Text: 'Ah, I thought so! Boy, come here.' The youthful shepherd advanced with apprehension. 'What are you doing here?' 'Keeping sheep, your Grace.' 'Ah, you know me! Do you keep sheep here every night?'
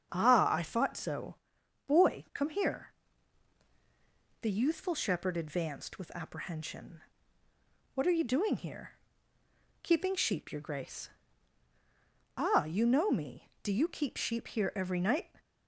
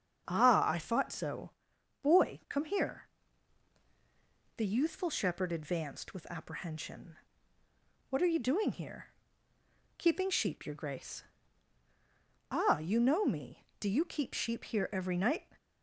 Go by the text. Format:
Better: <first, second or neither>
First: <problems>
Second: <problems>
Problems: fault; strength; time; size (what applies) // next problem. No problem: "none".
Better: neither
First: starts louder than the rest; strong; until 1.1 s; 7.5 dB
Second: starts louder than the rest; strong; until 1.3 s; 7.5 dB